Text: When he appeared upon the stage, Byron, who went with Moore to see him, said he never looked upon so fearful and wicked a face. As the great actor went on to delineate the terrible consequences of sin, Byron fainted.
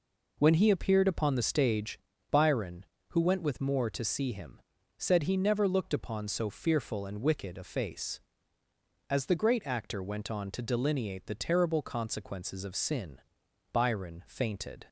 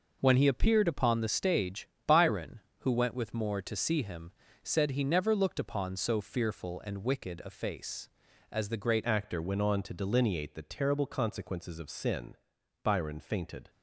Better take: first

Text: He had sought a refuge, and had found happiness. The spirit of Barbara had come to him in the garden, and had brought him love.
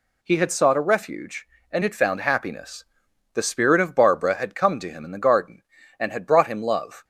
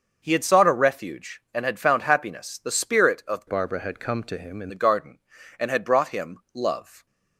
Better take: first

